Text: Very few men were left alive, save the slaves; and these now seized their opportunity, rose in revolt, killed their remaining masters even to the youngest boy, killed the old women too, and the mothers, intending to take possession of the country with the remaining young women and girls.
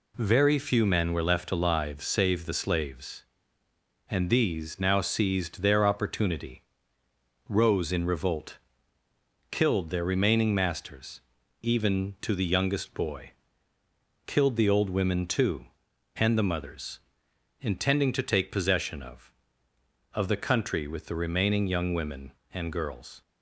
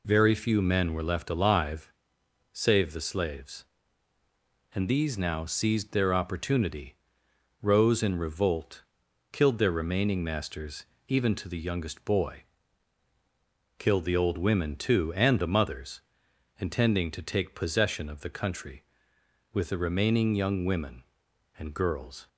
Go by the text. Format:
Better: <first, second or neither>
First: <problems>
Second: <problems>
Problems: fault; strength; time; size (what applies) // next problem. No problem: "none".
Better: second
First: pauses between "masters" and "even"; at 11.1 s; 0.42 s long // says "of" twice; at 20.1 s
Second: pauses between "masters" and "even"; slight; at 10.8 s; 0.22 s long